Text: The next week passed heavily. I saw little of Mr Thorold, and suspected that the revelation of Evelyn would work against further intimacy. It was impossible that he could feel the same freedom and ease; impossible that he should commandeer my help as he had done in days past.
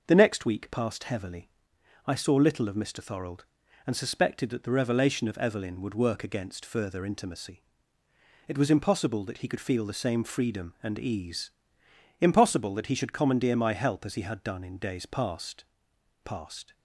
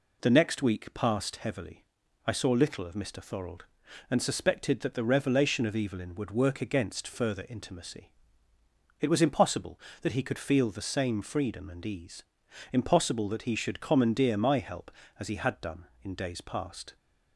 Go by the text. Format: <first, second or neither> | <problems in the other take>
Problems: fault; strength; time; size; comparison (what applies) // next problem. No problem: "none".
second | says "past" twice; at 16.2 s